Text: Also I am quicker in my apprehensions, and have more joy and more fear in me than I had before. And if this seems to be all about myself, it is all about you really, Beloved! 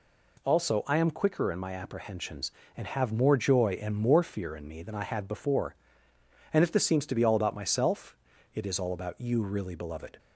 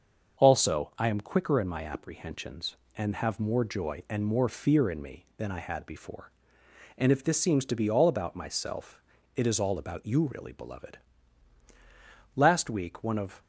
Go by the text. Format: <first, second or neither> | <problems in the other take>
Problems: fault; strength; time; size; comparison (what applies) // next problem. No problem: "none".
first | starts louder than the rest; until 1.4 s; 6.5 dB // goes on to say "Last week one of"; noticeable; from 12.3 s on; 1.0 s long